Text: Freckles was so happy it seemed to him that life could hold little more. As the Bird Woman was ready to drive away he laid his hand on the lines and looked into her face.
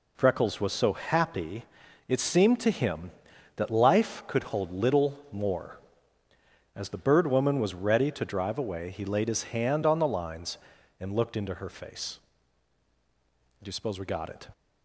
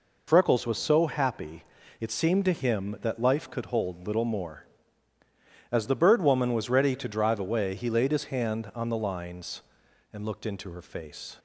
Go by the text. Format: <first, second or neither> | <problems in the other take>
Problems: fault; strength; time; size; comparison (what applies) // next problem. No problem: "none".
second | pauses between "happy" and "it"; at 1.6 s; 0.44 s long; slight in the second // goes on to say "Do you suppose we got it"; noticeable; from 13.6 s on; 0.86 s long